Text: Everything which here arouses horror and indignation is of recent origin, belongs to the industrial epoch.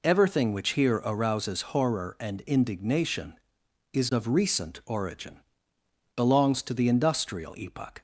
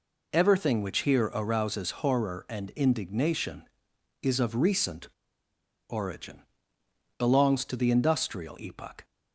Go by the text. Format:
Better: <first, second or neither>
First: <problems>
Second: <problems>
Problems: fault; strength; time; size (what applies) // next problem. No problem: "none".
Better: first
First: none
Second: pauses between "recent" and "origin"; noticeable; at 5.0 s; 0.81 s long